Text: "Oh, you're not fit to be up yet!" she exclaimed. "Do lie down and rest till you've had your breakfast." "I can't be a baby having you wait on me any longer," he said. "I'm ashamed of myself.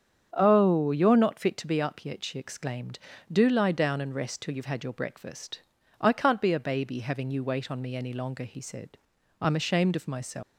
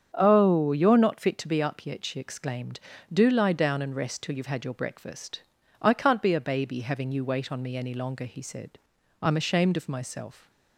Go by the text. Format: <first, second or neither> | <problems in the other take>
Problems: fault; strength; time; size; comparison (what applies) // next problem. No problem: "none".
second | starts louder than the rest; strong; until 1.3 s; 8 dB; strong in the second // leaves "myself" unfinished; at 10.4 s; 260 ms